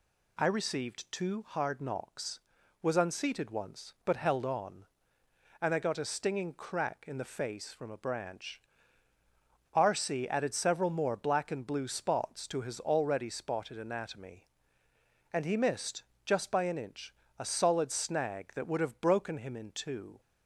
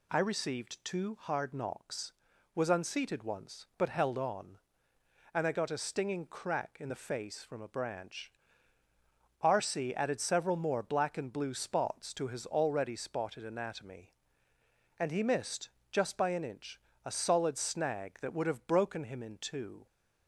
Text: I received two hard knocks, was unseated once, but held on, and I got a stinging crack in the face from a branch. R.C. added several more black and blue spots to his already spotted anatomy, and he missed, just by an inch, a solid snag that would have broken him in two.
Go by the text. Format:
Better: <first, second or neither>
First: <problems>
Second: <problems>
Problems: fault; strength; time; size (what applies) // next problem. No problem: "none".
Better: neither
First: none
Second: none